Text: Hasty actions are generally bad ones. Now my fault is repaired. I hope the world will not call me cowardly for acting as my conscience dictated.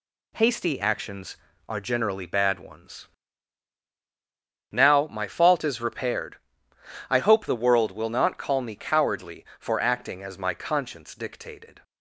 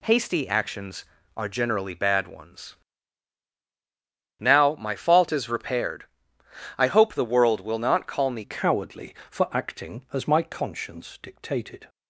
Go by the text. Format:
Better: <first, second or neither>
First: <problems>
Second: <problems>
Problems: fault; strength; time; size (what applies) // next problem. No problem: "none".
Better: first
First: none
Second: changes voice at "cowardly"; from 8.4 s on; 3.4 s long